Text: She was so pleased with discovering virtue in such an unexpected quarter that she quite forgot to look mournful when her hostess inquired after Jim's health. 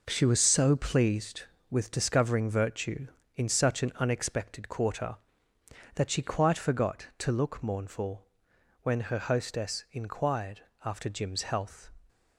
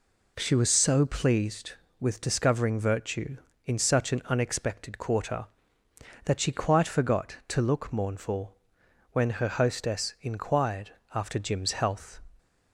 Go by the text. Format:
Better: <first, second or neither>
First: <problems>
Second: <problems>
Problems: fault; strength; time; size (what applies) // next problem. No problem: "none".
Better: second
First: gets quieter; strong; throughout; 8 dB // pauses between "mournful" and "when"; noticeable; at 8.2 s; 0.58 s long // pauses between "inquired" and "after"; slight; at 10.6 s; 0.18 s long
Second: pauses between "mournful" and "when"; noticeable; at 8.5 s; 0.58 s long // pauses between "inquired" and "after"; slight; at 10.9 s; 0.18 s long